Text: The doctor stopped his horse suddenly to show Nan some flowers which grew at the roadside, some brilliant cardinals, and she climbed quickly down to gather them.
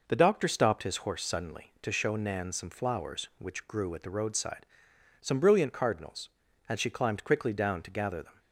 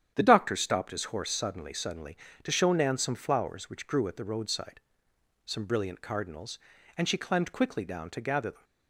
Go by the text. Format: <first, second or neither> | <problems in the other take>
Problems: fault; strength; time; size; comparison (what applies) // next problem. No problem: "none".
first | starts louder than the rest; strong; until 1.1 s; 9.5 dB // says "suddenly" twice; at 1.7 s